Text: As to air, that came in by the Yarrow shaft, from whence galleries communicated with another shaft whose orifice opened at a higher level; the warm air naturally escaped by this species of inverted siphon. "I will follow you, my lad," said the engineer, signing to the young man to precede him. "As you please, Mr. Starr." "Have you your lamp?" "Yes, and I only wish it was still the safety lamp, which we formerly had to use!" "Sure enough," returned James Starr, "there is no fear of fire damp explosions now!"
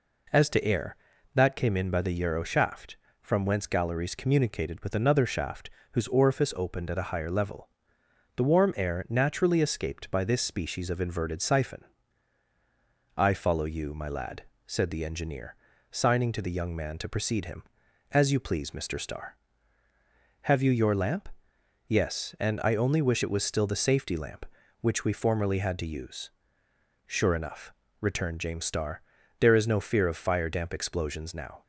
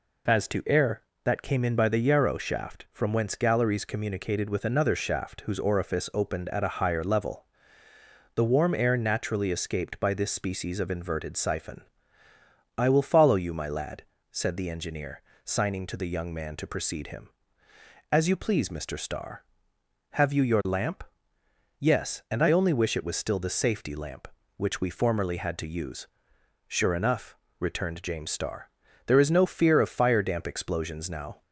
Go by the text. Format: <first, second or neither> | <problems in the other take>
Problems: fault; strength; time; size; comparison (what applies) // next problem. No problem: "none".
second | pauses between "shaft" and "whose"; slight; at 5.7 s; 0.22 s long // skips "will"; at 13.3 s